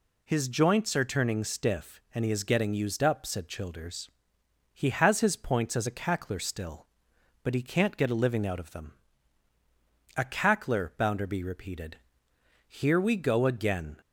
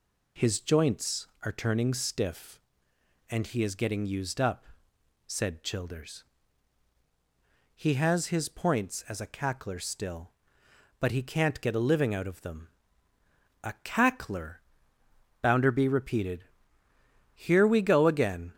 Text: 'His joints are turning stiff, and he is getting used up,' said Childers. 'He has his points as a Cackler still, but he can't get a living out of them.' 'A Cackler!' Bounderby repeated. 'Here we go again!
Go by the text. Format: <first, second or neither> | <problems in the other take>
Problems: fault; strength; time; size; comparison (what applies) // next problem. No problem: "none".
neither | none